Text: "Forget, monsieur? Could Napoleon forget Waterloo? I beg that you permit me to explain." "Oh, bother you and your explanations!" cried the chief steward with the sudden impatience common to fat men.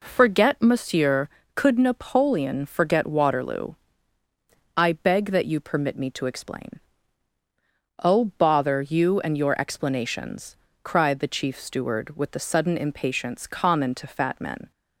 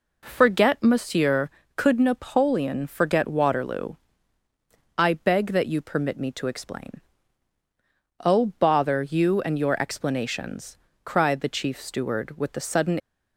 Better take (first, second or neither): first